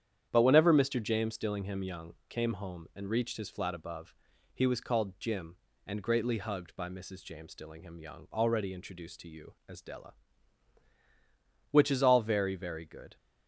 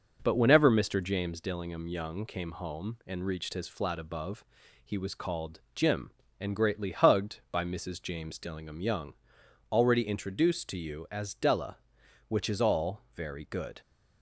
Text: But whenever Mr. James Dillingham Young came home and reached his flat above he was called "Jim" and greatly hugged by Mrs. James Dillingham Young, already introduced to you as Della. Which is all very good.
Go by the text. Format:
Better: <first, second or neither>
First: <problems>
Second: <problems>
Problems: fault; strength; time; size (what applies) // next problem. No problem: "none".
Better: second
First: starts louder than the rest; strong; until 1.3 s; 9 dB // pauses between "above" and "he"; at 4.1 s; 0.40 s long // says "very" twice; at 12.5 s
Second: pauses between "above" and "he"; at 4.4 s; 0.40 s long